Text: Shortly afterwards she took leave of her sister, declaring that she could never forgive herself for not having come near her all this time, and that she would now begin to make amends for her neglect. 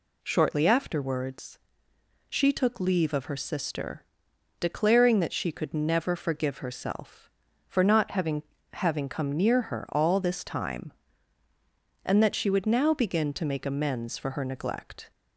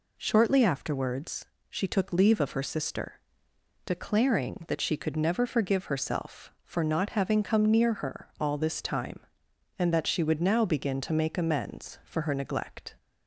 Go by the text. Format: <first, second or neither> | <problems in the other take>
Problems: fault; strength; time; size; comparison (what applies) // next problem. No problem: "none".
second | pauses between "afterwards" and "she"; noticeable; at 1.5 s; 0.70 s long; slight in the second // says "having" twice; at 8.7 s